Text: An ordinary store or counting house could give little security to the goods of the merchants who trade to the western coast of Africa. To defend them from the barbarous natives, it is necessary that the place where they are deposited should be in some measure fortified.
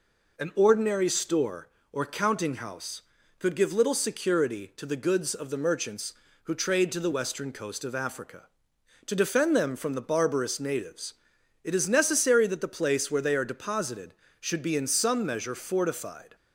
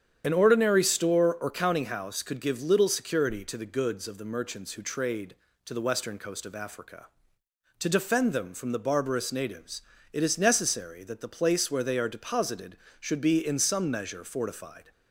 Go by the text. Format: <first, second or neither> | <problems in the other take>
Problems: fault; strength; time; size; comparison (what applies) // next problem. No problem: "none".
first | loses the start of "An"; at 0.2 s; 35 ms // starts louder than the rest; strong; until 1.2 s; 9 dB